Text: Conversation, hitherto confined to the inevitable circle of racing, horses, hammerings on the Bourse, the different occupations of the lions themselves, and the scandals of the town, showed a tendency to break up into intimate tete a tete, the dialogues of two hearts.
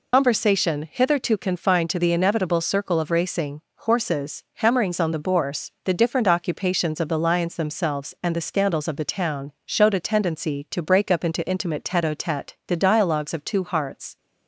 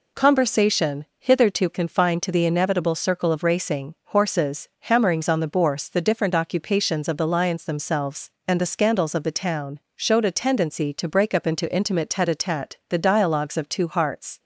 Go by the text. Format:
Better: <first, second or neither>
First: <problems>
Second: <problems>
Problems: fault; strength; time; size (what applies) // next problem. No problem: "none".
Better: second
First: loses the start of "Conversation"; at 0.1 s; 90 ms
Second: none